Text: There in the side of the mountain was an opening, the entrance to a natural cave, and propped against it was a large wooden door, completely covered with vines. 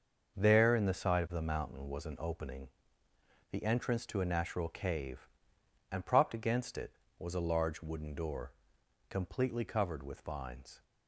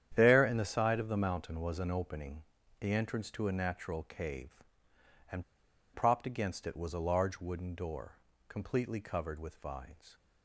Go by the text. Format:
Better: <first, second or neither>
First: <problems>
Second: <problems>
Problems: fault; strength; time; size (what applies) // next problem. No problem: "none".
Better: first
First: starts louder than the rest; until 1.4 s; 6 dB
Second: starts louder than the rest; strong; until 1.1 s; 9.5 dB // pauses between "and" and "propped"; noticeable; at 5.4 s; 0.50 s long